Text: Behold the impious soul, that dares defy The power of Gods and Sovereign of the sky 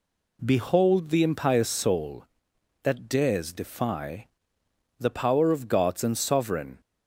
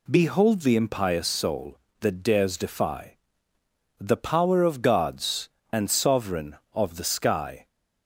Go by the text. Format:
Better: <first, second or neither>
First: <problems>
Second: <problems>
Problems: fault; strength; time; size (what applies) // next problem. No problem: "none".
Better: second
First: pauses between "defy" and "The"; noticeable; at 4.2 s; 0.72 s long // stops before "of the sky"; at 6.8 s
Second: pauses between "defy" and "The"; noticeable; at 3.1 s; 0.82 s long